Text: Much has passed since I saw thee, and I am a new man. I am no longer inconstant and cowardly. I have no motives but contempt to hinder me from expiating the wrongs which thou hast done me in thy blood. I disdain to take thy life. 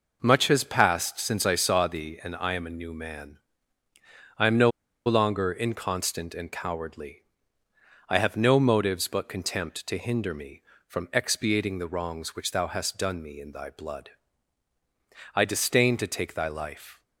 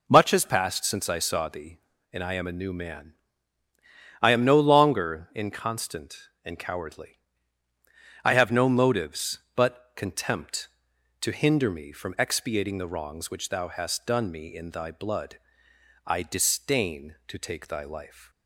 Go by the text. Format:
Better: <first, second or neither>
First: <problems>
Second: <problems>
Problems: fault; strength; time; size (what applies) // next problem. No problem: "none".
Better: second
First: pauses between "no" and "longer"; slight; at 4.7 s; 0.35 s long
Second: none